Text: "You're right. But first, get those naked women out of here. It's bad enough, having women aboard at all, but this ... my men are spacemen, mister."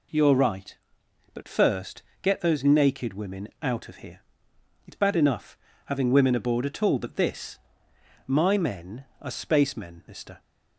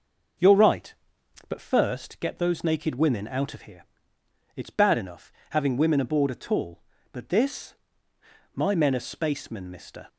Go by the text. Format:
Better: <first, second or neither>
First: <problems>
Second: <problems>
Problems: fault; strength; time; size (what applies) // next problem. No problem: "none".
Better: neither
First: none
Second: none